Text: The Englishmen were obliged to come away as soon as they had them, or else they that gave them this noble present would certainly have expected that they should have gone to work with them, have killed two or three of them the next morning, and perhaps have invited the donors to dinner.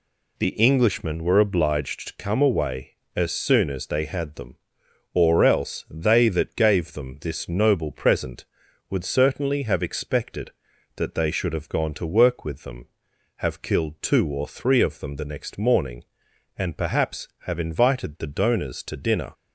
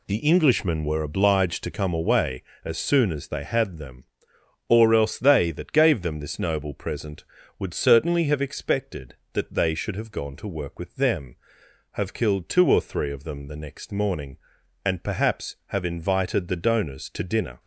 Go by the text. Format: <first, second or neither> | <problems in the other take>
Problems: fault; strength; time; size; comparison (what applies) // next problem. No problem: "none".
neither | none